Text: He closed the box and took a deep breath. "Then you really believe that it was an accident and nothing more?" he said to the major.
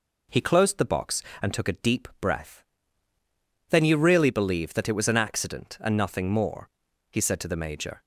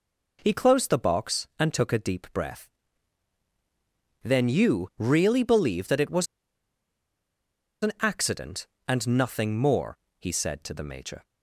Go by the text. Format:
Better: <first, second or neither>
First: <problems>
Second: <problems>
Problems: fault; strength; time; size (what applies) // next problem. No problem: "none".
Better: first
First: none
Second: pauses between "was" and "an"; strong; at 6.2 s; 1.5 s long